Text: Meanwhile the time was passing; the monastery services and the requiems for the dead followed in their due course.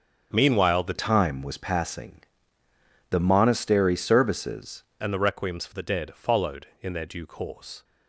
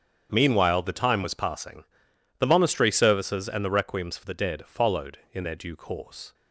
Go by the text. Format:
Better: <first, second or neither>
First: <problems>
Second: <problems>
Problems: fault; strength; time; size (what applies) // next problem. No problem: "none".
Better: second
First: starts louder than the rest; strong; until 1.3 s; 7.5 dB // changes voice from "time" to "services"; from 0.9 to 4.8 s; 3.9 s long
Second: starts louder than the rest; strong; until 1.3 s; 8 dB